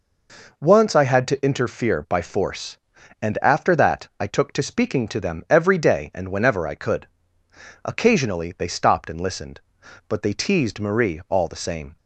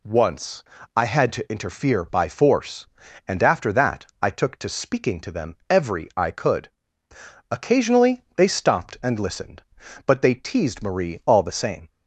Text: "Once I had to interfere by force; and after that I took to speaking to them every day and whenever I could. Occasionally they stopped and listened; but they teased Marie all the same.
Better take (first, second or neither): first